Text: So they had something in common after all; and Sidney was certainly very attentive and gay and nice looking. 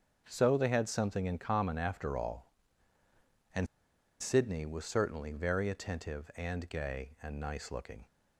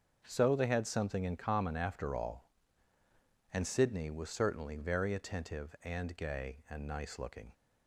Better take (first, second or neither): second